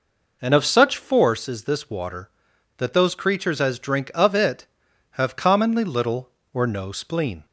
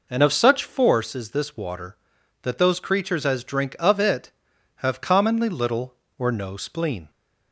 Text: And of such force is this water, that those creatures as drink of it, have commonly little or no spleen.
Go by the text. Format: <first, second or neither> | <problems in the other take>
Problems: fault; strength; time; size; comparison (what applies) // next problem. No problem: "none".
neither | none